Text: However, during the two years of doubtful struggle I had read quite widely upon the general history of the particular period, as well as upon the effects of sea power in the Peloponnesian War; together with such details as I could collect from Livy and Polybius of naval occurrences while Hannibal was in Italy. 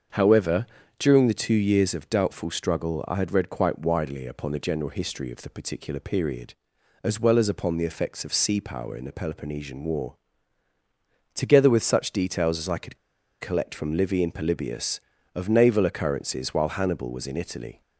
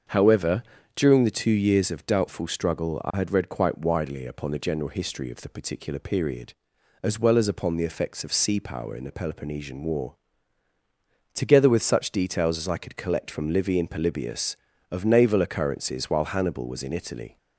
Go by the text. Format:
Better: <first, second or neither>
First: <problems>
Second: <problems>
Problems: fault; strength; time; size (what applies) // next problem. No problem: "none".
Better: second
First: starts louder than the rest; until 1.4 s; 7 dB // pauses between "could" and "collect"; at 12.9 s; 0.43 s long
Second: starts louder than the rest; until 1.4 s; 7 dB